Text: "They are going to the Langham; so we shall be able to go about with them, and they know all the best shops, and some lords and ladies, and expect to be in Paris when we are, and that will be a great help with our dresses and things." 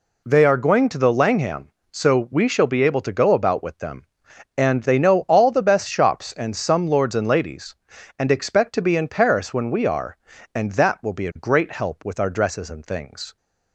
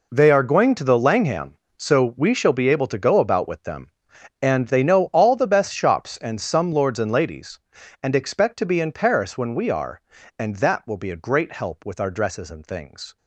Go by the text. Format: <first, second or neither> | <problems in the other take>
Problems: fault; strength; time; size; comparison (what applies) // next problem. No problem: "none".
first | gets quieter; strong; throughout; 12.5 dB